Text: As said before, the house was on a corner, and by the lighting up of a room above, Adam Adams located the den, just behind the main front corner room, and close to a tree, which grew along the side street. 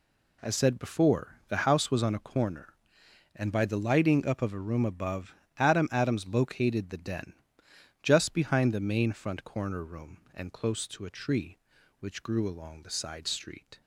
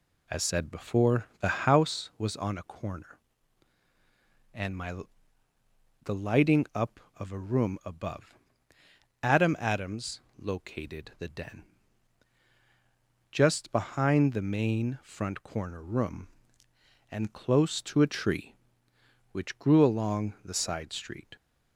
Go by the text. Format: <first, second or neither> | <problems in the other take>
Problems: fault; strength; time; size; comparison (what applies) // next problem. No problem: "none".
first | says "my" for "by"; at 4.7 s // pauses between "Adams" and "located"; slight; at 10.2 s; 0.18 s long